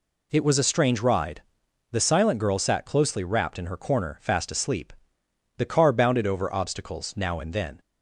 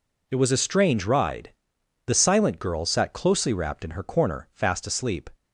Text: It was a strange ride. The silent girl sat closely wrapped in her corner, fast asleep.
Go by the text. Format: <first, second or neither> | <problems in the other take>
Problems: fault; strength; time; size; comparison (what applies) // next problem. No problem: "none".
second | goes on to say "The car bounded over obstacles now and then"; strong; from 5.5 s on; 2.2 s long